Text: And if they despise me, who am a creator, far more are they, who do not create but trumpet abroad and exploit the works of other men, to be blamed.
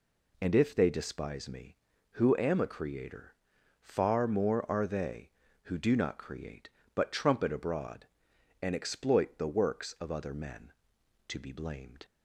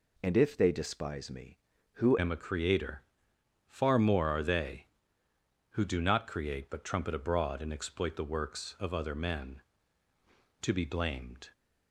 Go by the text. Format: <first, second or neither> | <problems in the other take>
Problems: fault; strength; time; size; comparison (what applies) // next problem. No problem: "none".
first | changes voice at "am"; from 2.1 s on; 9.4 s long